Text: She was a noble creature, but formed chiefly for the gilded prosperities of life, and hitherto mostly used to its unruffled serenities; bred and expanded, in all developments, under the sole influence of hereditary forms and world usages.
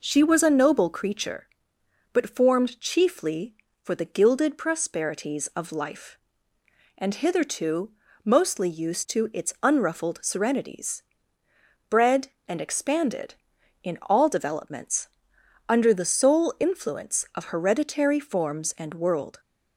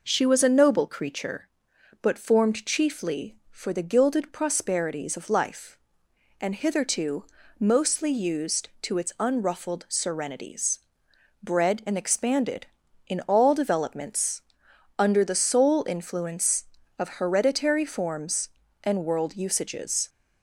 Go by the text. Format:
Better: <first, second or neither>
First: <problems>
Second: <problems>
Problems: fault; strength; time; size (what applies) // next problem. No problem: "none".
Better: second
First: pauses between "hitherto" and "mostly"; slight; at 7.9 s; 0.34 s long // stops before "usages"; at 19.3 s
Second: pauses between "hitherto" and "mostly"; at 7.2 s; 0.36 s long